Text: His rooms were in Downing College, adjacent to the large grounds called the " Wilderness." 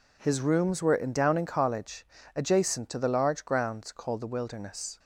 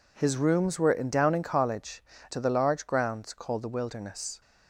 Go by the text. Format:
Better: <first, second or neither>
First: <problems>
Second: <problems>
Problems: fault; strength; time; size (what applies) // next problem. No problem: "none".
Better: first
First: none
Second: skips "adjacent"; at 2.1 s